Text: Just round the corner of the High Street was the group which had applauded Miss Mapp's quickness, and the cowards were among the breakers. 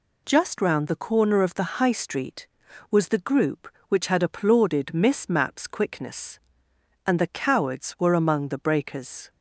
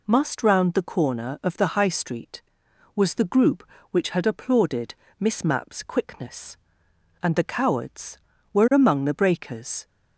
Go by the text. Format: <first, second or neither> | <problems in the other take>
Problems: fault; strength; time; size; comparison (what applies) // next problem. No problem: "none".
first | says "Must" for "Just"; at 0.0 s // pauses between "applauded" and "Miss"; slight; at 4.9 s; 0.24 s long